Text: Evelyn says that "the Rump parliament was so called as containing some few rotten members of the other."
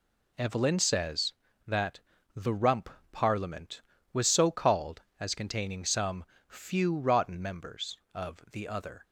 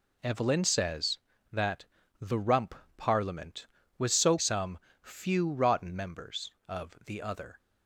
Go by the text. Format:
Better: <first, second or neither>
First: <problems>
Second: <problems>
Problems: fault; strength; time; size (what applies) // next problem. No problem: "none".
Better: first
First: pauses between "that" and "the"; slight; at 1.9 s; 0.34 s long // pauses between "Rump" and "parliament"; slight; at 2.8 s; 0.22 s long // pauses between "some" and "few"; slight; at 6.2 s; 0.24 s long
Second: pauses between "that" and "the"; slight; at 1.8 s; 0.34 s long // pauses between "Rump" and "parliament"; slight; at 2.7 s; 0.22 s long // skips "called as containing"; at 4.3 s // pauses between "some" and "few"; slight; at 4.7 s; 0.24 s long